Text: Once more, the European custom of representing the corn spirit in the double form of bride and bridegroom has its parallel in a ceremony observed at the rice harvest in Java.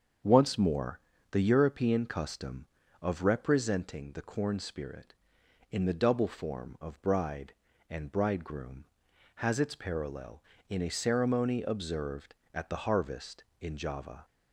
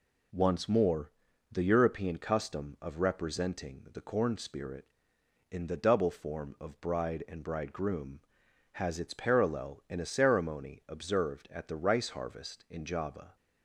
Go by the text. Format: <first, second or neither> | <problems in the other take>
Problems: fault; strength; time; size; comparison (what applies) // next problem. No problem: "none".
second | starts louder than the rest; strong; until 1.5 s; 7.5 dB // skips "rice"; at 12.8 s